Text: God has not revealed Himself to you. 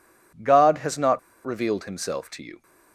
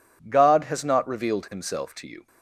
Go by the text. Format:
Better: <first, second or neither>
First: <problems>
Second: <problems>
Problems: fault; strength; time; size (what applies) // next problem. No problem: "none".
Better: second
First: pauses between "not" and "revealed"; slight; at 1.1 s; 0.26 s long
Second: none